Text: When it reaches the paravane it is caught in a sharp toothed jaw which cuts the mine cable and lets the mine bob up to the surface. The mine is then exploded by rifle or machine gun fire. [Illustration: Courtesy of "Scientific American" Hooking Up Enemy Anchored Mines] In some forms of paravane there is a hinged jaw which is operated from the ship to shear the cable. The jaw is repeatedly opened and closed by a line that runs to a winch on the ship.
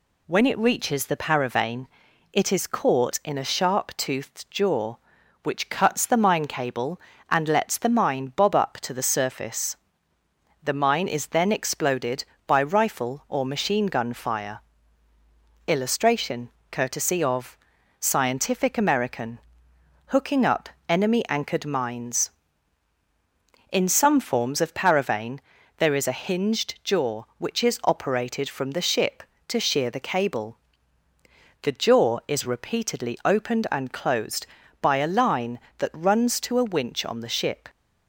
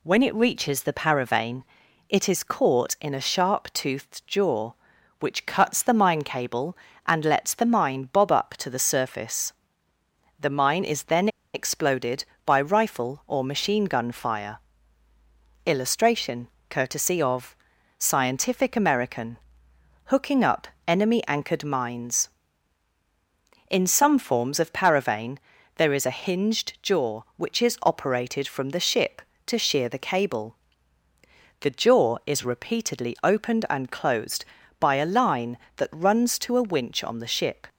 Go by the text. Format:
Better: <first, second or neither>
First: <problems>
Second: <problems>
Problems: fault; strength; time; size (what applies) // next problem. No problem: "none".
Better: first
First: pauses between "paravane" and "it"; noticeable; at 1.8 s; 0.46 s long // pauses between "of" and "Scientific"; at 17.5 s; 0.44 s long // pauses between "American" and "Hooking"; noticeable; at 19.3 s; 0.68 s long // pauses between "Up" and "Enemy"; slight; at 20.6 s; 0.20 s long // pauses between "paravane" and "there"; at 25.3 s; 0.38 s long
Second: pauses between "paravane" and "it"; noticeable; at 1.6 s; 0.46 s long // pauses between "then" and "exploded"; slight; at 11.2 s; 0.26 s long // pauses between "of" and "Scientific"; at 17.5 s; 0.44 s long // pauses between "American" and "Hooking"; noticeable; at 19.3 s; 0.68 s long // pauses between "Up" and "Enemy"; slight; at 20.6 s; 0.20 s long // pauses between "paravane" and "there"; at 25.3 s; 0.38 s long